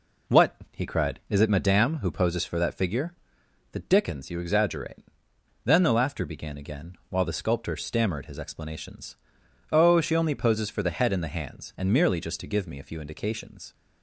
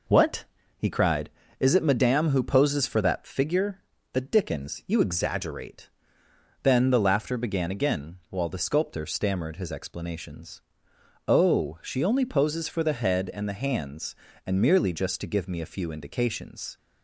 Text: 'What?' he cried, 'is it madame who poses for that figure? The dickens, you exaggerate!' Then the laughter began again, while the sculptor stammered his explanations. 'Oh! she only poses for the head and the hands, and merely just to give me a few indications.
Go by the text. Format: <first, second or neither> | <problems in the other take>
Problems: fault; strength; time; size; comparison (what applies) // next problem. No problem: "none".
neither | none